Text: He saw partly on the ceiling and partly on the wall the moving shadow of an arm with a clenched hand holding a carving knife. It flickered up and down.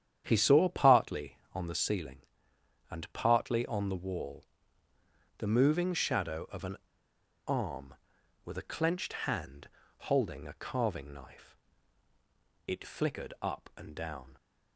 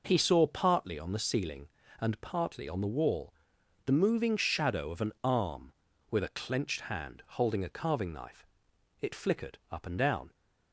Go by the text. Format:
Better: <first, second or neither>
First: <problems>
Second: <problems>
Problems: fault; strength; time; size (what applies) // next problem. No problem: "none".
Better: second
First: starts louder than the rest; strong; until 1.2 s; 9.5 dB // pauses between "wall" and "the"; noticeable; at 4.4 s; 0.94 s long // pauses between "an" and "arm"; noticeable; at 6.7 s; 0.70 s long // pauses between "hand" and "holding"; at 9.6 s; 0.42 s long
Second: pauses between "wall" and "the"; noticeable; at 3.3 s; 0.52 s long